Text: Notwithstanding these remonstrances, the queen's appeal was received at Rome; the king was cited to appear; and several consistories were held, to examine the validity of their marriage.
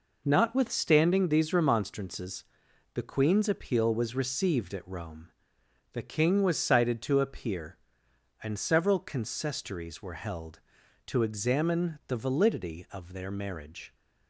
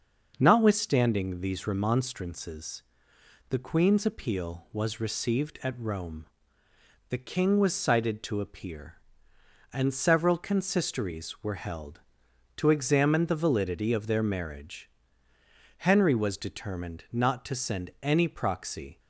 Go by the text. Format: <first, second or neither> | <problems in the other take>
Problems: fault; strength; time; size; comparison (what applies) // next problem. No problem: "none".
first | starts louder than the rest; until 1.3 s; 6.5 dB // goes on to say "Henry was determined not to send any proxy"; strong; from 15.7 s on; 3.2 s long